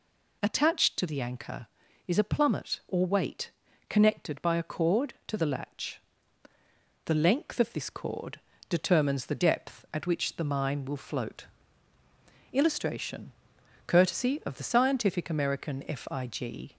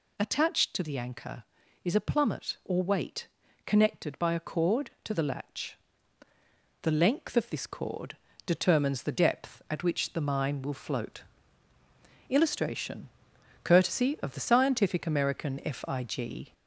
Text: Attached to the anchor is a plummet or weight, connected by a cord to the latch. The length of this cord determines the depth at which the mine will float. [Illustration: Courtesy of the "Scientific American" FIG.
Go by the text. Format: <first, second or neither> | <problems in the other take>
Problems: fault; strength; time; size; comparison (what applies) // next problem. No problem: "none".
first | gets louder; slight; throughout; 3 dB // pauses between "cord" and "determines"; slight; at 8.1 s; 0.30 s long; slight in the first